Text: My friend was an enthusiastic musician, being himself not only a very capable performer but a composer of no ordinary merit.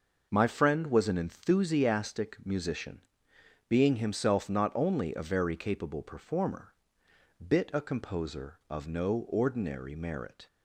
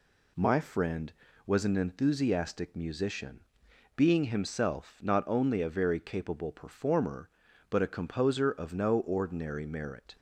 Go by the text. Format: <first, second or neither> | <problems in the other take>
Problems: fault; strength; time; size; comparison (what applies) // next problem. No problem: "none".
second | says "bit" for "but"; at 7.4 s